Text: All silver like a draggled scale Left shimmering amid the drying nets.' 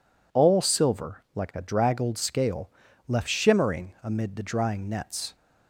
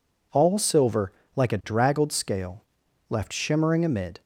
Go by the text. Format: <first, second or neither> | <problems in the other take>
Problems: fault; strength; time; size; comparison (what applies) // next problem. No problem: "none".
first | pauses between "silver" and "like"; slight; at 1.1 s; 0.24 s long // pauses between "scale" and "Left"; noticeable; at 2.6 s; 0.46 s long; slight in the first // stops before "the drying nets"; at 4.2 s